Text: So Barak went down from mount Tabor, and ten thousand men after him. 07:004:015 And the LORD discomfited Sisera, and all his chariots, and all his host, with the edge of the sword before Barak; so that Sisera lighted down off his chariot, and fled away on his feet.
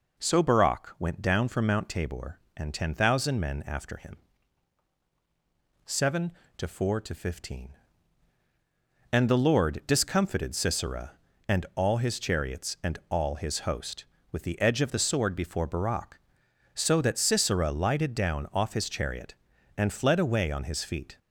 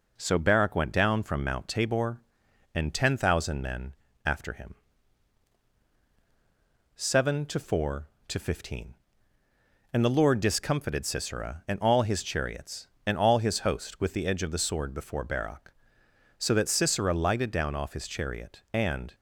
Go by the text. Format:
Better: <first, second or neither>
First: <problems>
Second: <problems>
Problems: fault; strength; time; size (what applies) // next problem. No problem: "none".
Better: first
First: none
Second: pauses between "men" and "after"; slight; at 3.9 s; 0.32 s long // stops before "fled away on his feet"; at 19.1 s